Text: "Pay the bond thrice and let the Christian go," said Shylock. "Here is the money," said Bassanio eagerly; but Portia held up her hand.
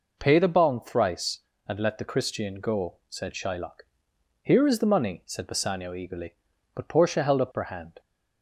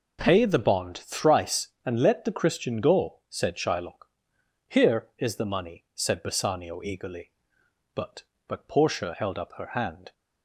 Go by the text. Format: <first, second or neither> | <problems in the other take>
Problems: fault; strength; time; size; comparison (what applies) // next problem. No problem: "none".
first | says "but" twice; at 8.4 s